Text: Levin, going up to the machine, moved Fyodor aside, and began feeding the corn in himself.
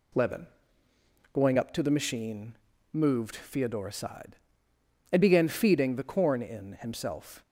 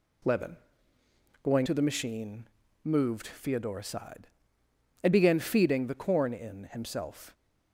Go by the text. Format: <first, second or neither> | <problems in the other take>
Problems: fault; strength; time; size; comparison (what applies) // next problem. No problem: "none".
first | skips "up"; at 1.6 s